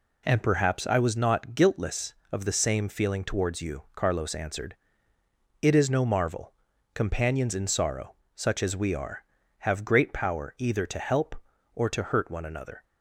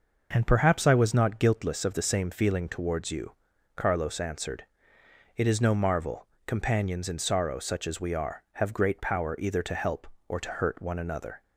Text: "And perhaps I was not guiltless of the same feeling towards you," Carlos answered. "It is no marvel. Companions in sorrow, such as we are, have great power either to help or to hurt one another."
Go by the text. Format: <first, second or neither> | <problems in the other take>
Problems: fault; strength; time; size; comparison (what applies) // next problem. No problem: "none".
neither | none